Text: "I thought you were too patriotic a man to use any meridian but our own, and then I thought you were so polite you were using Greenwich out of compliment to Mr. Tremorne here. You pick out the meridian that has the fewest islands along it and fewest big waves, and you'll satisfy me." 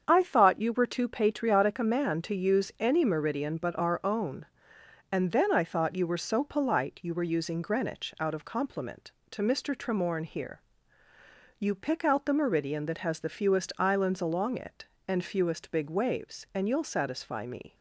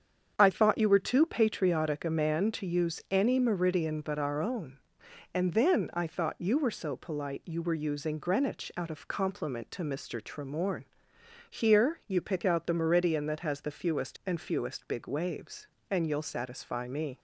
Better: first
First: starts louder than the rest; strong; until 1.0 s; 7.5 dB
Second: starts louder than the rest; strong; until 1.3 s; 7.5 dB // pauses between "Tremorne" and "here"; noticeable; at 10.8 s; 0.66 s long // skips "islands along it"; at 14.2 s

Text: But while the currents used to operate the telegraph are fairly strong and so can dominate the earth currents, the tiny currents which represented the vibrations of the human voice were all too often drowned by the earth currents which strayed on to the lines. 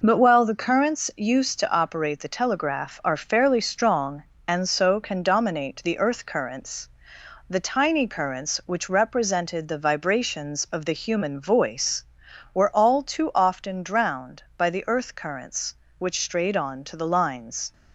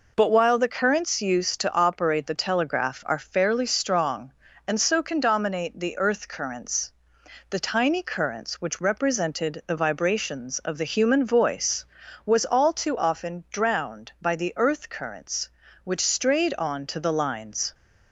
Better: first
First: none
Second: says "was" for "were"; at 12.2 s

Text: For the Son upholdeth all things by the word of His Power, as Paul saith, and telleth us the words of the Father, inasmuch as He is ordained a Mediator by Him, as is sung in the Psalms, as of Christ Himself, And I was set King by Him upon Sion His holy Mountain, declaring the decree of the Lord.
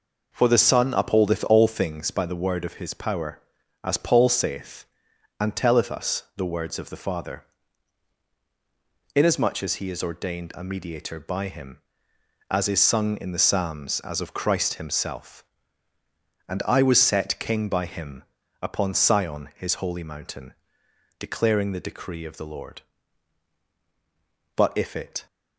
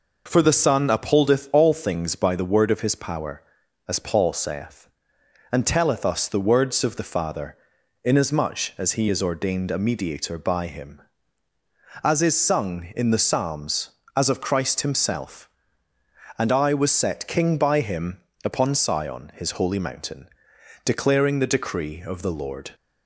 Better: second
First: pauses between "Him" and "upon"; at 18.2 s; 0.38 s long // goes on to say "But if it"; noticeable; from 24.5 s on; 0.70 s long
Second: pauses between "Him" and "upon"; slight; at 18.1 s; 0.26 s long

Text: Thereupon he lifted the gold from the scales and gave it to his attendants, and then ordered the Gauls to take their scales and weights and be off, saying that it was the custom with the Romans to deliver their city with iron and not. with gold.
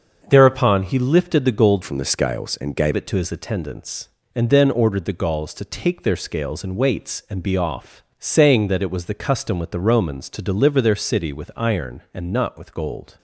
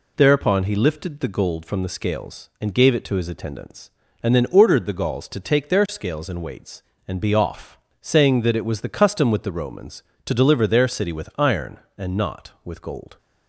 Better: second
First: starts louder than the rest; until 1.2 s; 6.5 dB // changes voice from "from" to "gave"; from 1.8 to 2.9 s; 1.1 s long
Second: none

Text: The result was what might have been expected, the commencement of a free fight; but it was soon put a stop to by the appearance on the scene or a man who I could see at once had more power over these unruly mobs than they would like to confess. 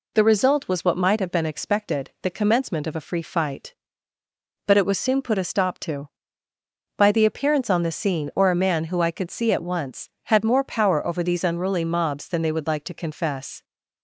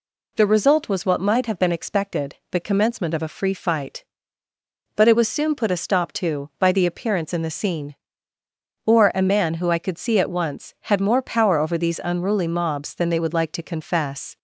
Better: first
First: none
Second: says "in" for "on"; at 7.3 s

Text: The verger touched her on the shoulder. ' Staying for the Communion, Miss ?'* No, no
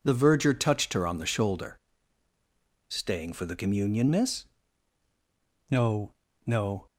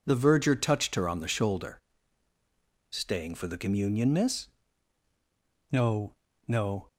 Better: neither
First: starts louder than the rest; until 1.0 s; 6.5 dB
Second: starts louder than the rest; until 1.0 s; 6.5 dB

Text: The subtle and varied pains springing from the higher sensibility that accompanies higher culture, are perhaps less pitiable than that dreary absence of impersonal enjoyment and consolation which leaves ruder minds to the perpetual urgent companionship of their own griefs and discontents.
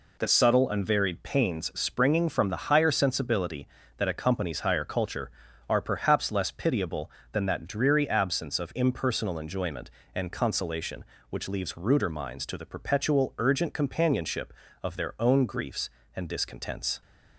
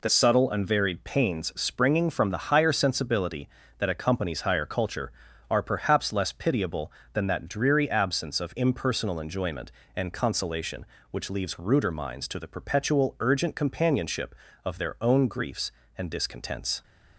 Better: neither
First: none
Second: none

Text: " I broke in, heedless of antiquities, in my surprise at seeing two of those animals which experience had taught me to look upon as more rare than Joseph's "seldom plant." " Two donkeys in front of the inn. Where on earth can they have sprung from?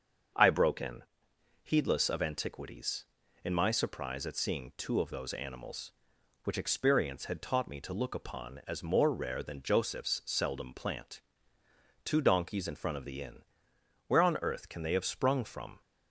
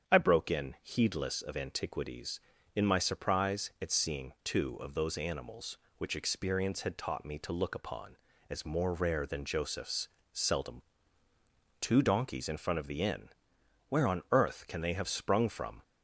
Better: first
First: starts louder than the rest; until 1.9 s; 6.5 dB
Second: starts louder than the rest; strong; until 1.1 s; 8 dB // pauses between "Joseph's" and "seldom"; slight; at 10.0 s; 0.22 s long // skips "plant"; at 11.0 s

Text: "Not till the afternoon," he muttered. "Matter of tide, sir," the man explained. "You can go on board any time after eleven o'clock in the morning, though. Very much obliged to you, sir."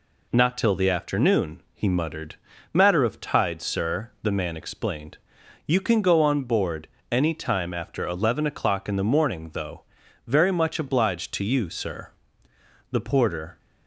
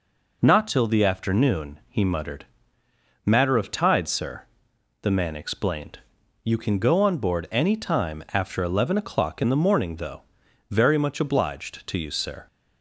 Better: second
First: pauses between "board" and "any"; slight; at 6.8 s; 0.24 s long // goes on to say "The porter"; noticeable; from 12.9 s on; 0.68 s long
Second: none

